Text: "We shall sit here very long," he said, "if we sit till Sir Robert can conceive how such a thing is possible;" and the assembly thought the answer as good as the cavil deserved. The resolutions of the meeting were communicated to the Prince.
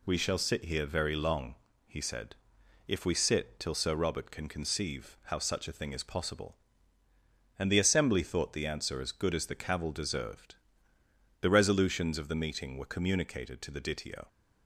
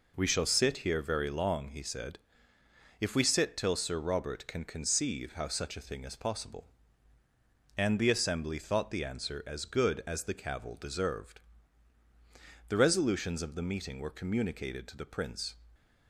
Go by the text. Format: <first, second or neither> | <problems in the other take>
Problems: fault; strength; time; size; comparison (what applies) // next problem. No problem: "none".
second | says "Ditio" for "Prince"; at 13.7 s